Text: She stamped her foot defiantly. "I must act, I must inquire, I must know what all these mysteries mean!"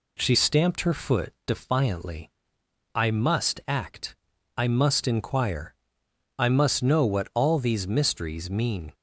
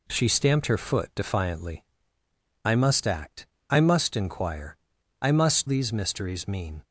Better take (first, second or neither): first